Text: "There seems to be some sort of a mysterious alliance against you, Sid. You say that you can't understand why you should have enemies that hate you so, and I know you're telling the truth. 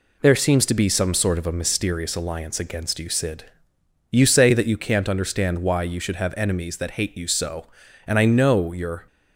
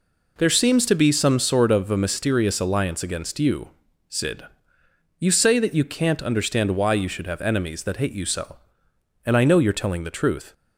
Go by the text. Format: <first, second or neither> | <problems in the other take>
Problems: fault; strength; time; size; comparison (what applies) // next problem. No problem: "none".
second | stops before "telling the truth"; at 9.0 s